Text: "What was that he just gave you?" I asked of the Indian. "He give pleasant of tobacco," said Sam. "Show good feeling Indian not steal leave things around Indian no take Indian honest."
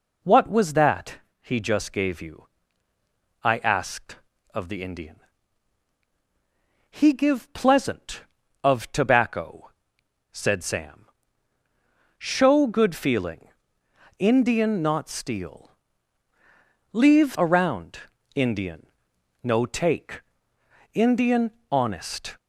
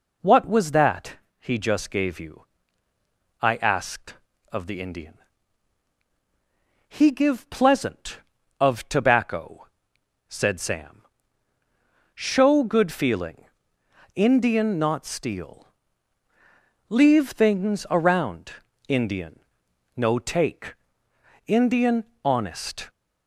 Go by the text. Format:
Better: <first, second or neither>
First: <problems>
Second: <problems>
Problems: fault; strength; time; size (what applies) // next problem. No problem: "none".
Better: second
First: pauses between "that" and "he"; slight; at 1.1 s; 0.24 s long // pauses between "feeling" and "Indian"; noticeable; at 13.4 s; 0.68 s long // pauses between "steal" and "leave"; at 15.7 s; 1.2 s long // skips "things"; at 17.3 s // pauses between "around" and "Indian"; at 17.9 s; 0.38 s long // pauses between "Indian" and "no"; noticeable; at 18.8 s; 0.56 s long // pauses between "take" and "Indian"; noticeable; at 20.2 s; 0.74 s long // pauses between "Indian" and "honest"; slight; at 21.5 s; 0.22 s long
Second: pauses between "that" and "he"; slight; at 1.1 s; 0.24 s long // pauses between "feeling" and "Indian"; noticeable; at 13.4 s; 0.68 s long // pauses between "steal" and "leave"; at 15.6 s; 1.2 s long // pauses between "around" and "Indian"; at 18.5 s; 0.38 s long // pauses between "Indian" and "no"; noticeable; at 19.3 s; 0.56 s long // pauses between "take" and "Indian"; noticeable; at 20.7 s; 0.74 s long // pauses between "Indian" and "honest"; slight; at 22.0 s; 0.22 s long